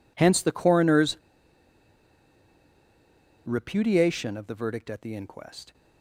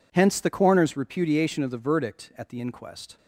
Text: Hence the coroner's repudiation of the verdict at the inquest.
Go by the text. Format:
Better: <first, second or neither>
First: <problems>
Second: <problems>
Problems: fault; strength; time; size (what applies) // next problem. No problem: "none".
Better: second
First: pauses between "coroner's" and "repudiation"; strong; at 1.1 s; 2.2 s long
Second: none